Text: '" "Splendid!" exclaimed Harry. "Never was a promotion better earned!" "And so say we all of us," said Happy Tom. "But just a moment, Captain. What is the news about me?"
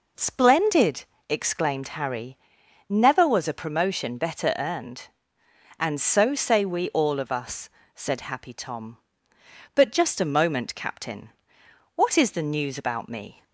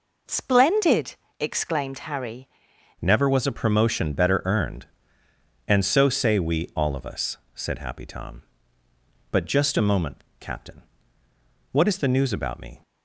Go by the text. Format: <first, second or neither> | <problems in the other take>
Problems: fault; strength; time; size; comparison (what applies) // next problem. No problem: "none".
first | changes voice at "Never"; from 2.9 s on; 9.9 s long